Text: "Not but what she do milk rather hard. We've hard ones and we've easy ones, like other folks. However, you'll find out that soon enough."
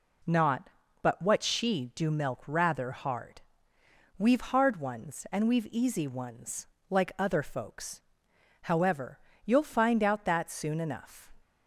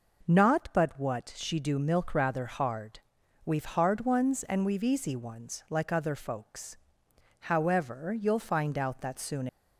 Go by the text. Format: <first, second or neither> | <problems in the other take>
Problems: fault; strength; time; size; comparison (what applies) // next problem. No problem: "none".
first | stops before "enough"; at 9.4 s